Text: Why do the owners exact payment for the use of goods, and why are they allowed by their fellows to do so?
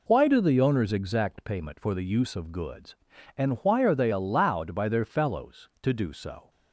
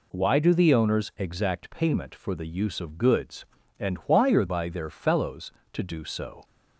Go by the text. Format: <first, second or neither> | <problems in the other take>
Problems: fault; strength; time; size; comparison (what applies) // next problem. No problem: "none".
first | skips "they allowed"; at 4.4 s